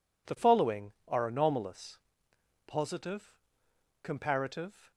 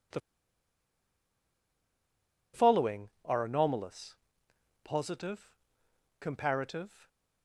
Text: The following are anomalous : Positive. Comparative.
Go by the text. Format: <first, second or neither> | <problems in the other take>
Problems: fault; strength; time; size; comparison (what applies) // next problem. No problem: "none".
first | pauses between "The" and "following"; strong; at 0.2 s; 2.3 s long